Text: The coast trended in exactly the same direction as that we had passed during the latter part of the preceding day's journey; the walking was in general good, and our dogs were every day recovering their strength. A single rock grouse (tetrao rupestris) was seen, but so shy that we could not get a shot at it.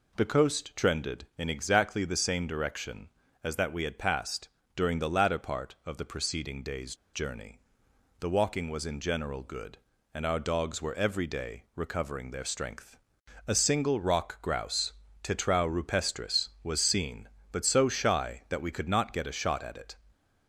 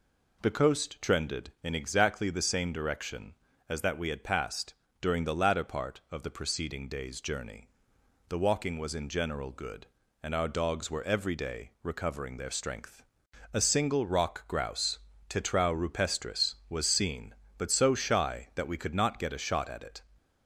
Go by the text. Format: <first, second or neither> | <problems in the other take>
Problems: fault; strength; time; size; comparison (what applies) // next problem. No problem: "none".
second | pauses between "passed" and "during"; slight; at 4.4 s; 0.28 s long; slight in the second // pauses between "day's" and "journey"; slight; at 6.9 s; 0.18 s long